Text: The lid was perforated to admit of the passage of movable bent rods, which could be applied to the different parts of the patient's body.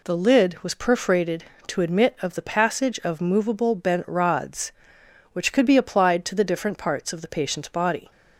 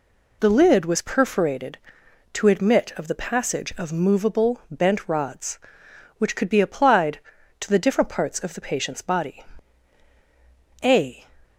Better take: first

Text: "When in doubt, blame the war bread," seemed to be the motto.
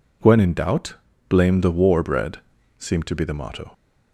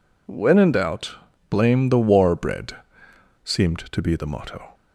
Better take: neither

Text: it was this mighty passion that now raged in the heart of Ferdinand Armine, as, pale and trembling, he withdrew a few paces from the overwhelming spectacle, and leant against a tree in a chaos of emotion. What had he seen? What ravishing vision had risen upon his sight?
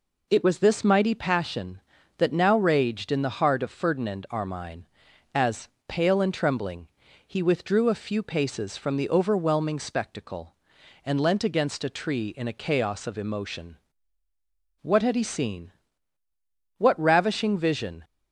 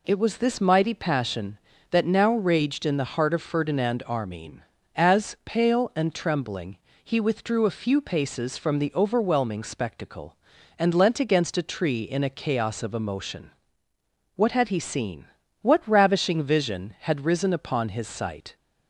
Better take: second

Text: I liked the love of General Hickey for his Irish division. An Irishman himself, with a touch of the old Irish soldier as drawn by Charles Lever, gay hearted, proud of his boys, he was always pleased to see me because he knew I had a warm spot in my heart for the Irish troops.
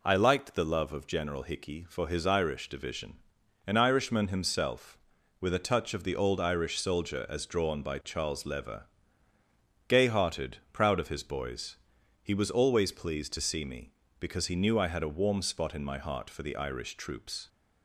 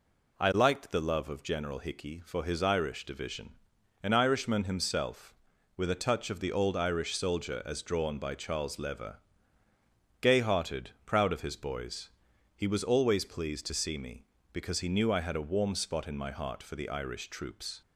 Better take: neither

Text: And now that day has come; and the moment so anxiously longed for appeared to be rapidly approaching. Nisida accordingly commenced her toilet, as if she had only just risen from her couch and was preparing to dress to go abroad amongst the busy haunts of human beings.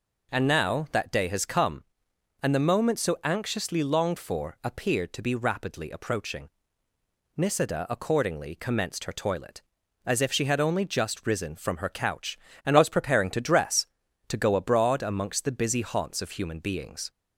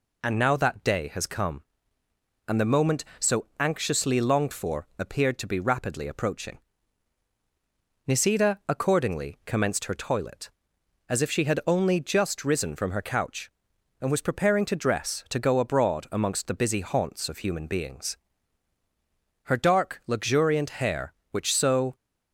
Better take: first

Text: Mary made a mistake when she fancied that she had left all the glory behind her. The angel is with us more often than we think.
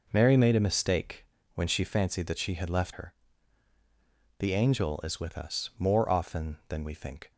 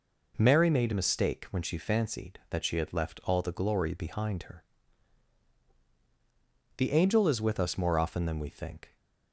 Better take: second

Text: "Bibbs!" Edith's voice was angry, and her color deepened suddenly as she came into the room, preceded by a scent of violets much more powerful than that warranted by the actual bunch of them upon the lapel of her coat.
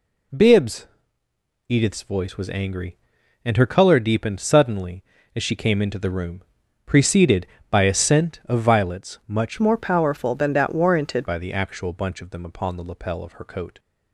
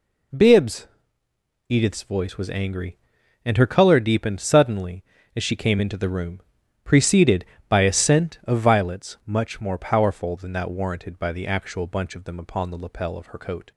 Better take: second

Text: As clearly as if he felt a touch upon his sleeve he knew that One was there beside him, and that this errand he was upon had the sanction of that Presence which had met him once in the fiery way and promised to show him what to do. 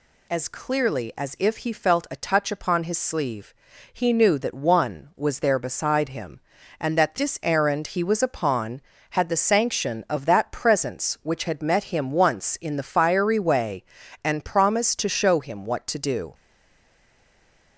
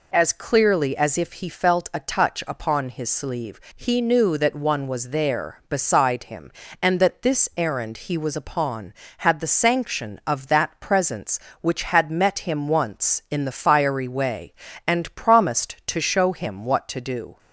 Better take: second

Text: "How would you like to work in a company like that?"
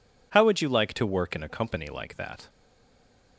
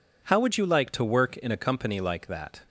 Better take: second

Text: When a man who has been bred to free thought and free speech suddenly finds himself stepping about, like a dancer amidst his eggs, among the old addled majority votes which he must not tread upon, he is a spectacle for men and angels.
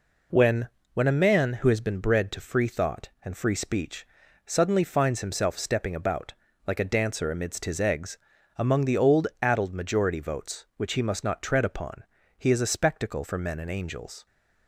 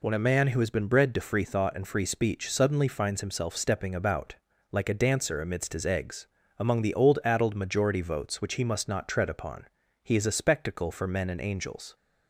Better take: second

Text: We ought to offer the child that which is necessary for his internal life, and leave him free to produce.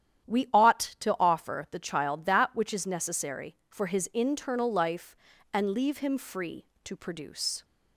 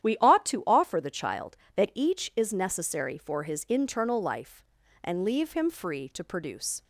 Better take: first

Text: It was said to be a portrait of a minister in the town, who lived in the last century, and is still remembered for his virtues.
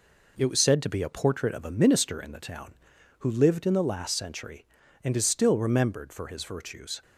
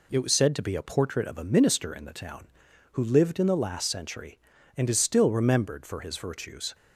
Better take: second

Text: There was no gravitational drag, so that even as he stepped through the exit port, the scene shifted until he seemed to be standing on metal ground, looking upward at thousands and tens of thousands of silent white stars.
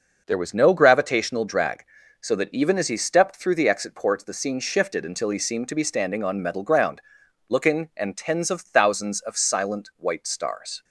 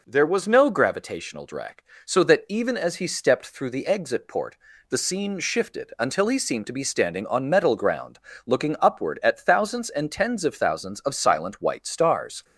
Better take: second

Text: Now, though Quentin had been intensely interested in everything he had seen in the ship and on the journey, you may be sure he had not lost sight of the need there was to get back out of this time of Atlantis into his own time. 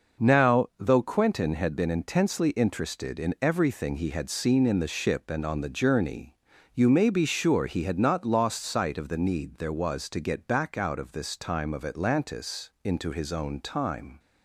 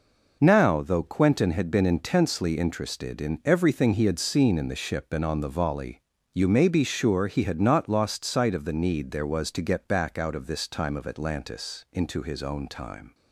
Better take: first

